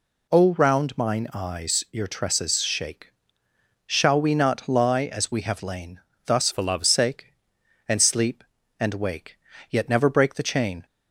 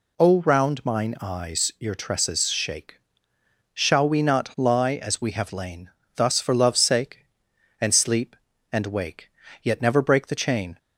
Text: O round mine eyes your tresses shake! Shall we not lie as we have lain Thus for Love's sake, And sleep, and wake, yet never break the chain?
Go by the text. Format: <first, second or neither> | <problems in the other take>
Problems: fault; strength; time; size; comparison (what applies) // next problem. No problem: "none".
second | pauses between "lain" and "Thus"; slight; at 6.0 s; 0.24 s long; slight in the second // changes voice from "for" to "Love's"; from 6.5 to 6.8 s; 0.3 s long